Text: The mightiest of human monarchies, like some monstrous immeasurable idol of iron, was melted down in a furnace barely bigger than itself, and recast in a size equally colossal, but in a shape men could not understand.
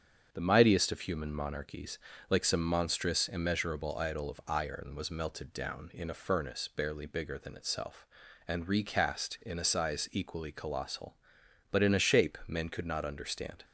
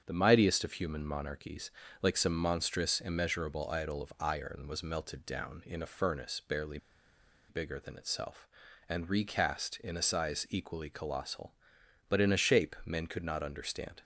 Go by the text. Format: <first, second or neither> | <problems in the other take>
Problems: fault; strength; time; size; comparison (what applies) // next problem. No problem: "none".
first | starts louder than the rest; strong; until 1.0 s; 7.5 dB; strong in the first // pauses between "barely" and "bigger"; noticeable; at 6.7 s; 0.71 s long